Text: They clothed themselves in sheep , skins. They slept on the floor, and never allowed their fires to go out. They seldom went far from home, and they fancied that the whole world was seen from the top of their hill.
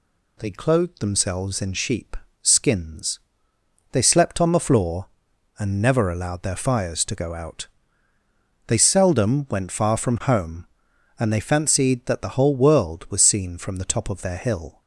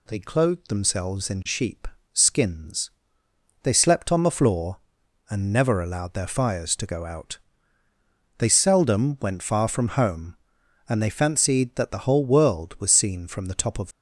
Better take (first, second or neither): first